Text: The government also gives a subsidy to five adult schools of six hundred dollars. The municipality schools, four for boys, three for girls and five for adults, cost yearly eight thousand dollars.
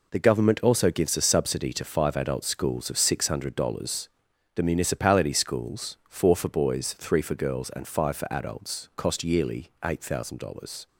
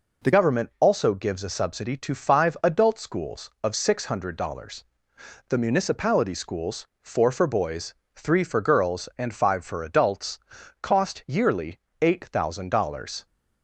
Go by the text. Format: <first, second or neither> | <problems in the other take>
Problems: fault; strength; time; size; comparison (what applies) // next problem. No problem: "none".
first | changes voice at "government"; from 0.3 s on; 12.9 s long // pauses between "yearly" and "eight"; slight; at 11.7 s; 0.20 s long